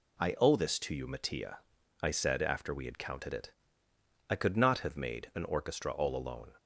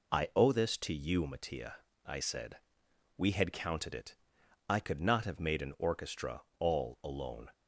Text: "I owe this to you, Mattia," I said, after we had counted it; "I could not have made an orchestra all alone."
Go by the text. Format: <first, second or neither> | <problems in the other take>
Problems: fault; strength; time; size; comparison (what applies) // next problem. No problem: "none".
first | skips "after"; at 2.8 s // pauses between "orchestra" and "all"; slight; at 6.4 s; 0.16 s long